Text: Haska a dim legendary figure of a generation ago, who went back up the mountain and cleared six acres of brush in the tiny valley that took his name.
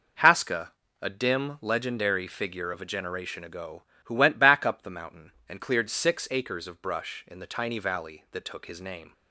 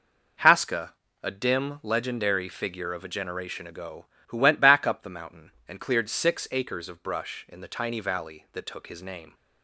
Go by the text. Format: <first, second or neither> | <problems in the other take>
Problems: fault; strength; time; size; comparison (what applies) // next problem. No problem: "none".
neither | pauses between "Haska" and "a"; slight; the same in both